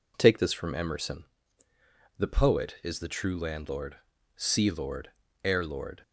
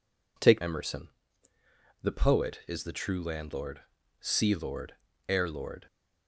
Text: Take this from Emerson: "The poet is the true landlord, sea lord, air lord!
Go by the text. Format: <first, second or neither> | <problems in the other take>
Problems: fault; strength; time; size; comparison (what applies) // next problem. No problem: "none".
first | skips "this from"; at 0.6 s